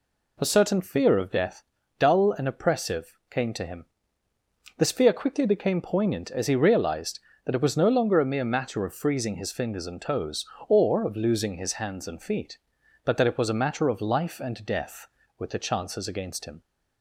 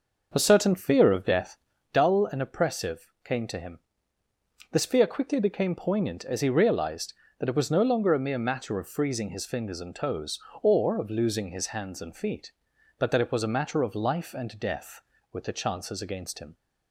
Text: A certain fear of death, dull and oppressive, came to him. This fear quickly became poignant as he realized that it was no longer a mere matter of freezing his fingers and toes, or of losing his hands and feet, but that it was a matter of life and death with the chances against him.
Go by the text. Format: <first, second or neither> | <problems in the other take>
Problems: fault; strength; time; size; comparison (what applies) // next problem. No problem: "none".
first | starts louder than the rest; noticeable; until 2.0 s; 6 dB